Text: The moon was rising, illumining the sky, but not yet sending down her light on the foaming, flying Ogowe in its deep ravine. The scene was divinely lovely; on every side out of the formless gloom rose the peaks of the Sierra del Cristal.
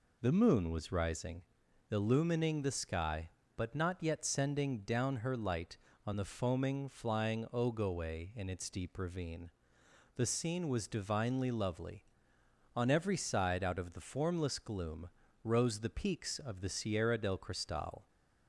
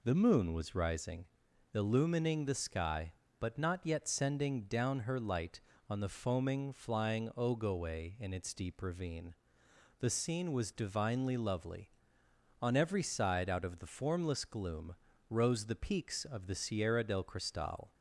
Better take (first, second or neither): neither